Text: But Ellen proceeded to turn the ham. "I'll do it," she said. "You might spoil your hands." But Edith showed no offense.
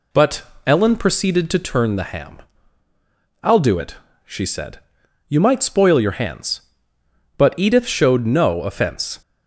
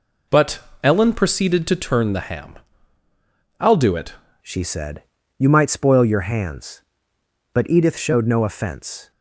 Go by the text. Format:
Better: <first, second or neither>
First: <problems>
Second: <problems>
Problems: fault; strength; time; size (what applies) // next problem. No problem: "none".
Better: first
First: pauses between "But" and "Ellen"; slight; at 0.4 s; 0.24 s long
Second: pauses between "But" and "Ellen"; slight; at 0.5 s; 0.24 s long // changes voice at "she"; from 4.4 s on; 4.7 s long